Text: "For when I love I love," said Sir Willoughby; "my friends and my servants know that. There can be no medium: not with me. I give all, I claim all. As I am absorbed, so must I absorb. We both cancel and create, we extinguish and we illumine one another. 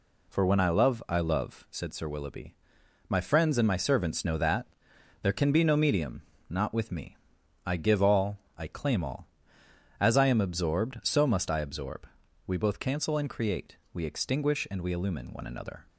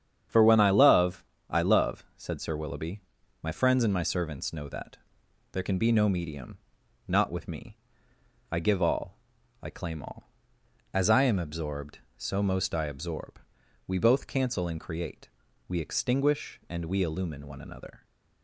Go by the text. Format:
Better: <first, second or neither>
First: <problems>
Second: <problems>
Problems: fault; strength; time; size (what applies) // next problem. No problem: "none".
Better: first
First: none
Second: starts louder than the rest; strong; until 1.5 s; 8.5 dB // pauses between "love" and "I"; slight; at 1.2 s; 0.26 s long // says "most" for "must"; at 12.4 s